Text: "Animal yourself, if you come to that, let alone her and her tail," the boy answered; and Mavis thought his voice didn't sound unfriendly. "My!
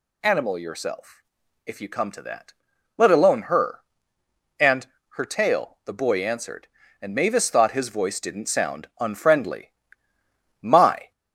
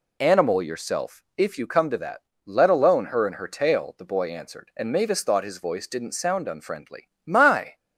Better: second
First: gets louder; slight; throughout; 2.5 dB // pauses between "and" and "her"; slight; at 4.8 s; 0.26 s long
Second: none

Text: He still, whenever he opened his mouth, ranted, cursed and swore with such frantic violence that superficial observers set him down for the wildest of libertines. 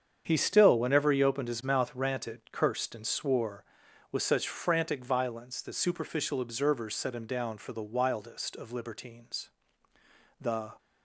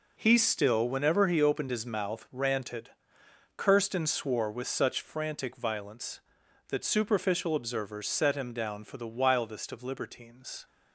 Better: second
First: starts louder than the rest; strong; until 1.2 s; 7.5 dB // goes on to say "The"; slight; from 10.4 s on; 0.30 s long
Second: none

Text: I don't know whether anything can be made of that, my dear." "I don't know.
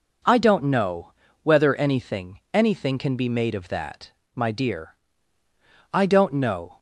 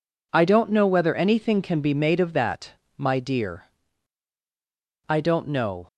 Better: second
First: pauses between "know" and "whether"; slight; at 1.1 s; 0.32 s long // says "anything" twice; at 2.5 s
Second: none

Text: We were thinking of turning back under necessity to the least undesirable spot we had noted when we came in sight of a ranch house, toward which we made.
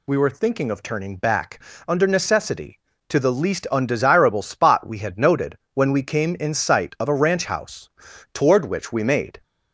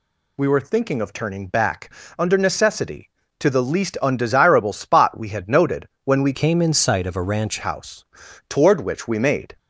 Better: first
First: pauses between "back" and "under"; slight; at 1.6 s; 0.24 s long // pauses between "noted" and "when"; slight; at 5.5 s; 0.18 s long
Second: pauses between "back" and "under"; slight; at 1.9 s; 0.24 s long // pauses between "noted" and "when"; slight; at 5.8 s; 0.18 s long // changes voice from "came" to "ranch"; from 6.3 to 7.5 s; 1.2 s long

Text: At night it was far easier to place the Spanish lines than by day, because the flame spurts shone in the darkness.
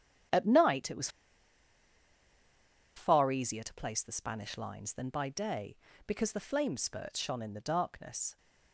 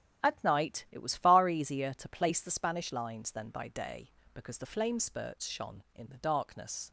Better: second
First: starts louder than the rest; strong; until 3.1 s; 10 dB // pauses between "was" and "far"; strong; at 1.0 s; 1.8 s long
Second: starts louder than the rest; strong; until 1.3 s; 10 dB

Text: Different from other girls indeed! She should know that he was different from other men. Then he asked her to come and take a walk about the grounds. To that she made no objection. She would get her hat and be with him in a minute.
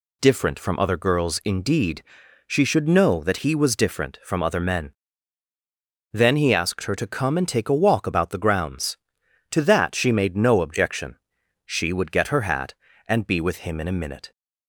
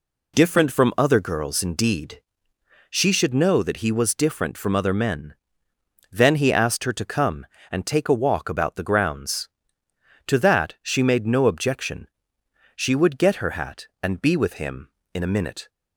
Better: neither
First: none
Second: none

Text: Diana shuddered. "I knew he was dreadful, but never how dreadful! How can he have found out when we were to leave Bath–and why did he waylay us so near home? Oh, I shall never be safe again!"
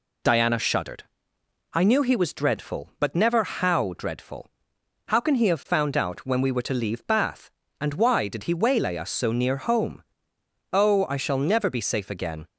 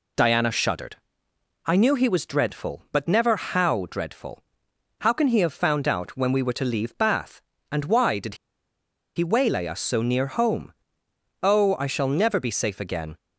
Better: first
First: none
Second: pauses between "did" and "he"; noticeable; at 8.3 s; 0.80 s long

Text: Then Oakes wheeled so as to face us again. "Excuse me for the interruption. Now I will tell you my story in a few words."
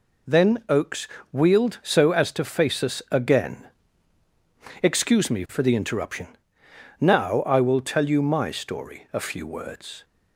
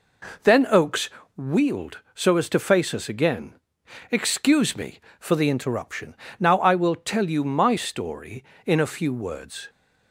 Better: second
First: pauses between "Oakes" and "wheeled"; slight; at 1.0 s; 0.24 s long // skips "in"; at 9.0 s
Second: pauses between "Oakes" and "wheeled"; slight; at 1.0 s; 0.26 s long

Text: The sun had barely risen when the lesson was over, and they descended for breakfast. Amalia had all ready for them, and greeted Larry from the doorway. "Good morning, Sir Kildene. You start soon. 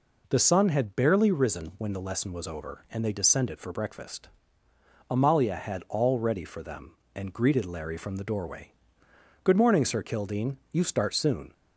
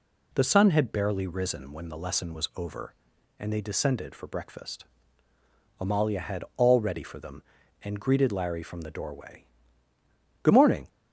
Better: first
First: none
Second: stops before "Sir Kildene You start soon"; at 10.8 s

